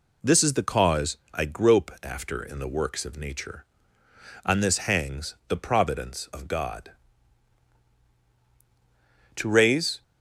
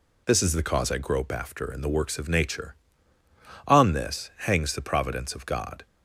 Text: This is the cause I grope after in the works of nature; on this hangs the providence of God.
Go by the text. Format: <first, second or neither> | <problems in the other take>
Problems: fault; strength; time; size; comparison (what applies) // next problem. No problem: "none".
second | pauses between "cause" and "I"; slight; at 1.1 s; 0.16 s long // goes on to say "To raise"; noticeable; from 9.3 s on; 0.66 s long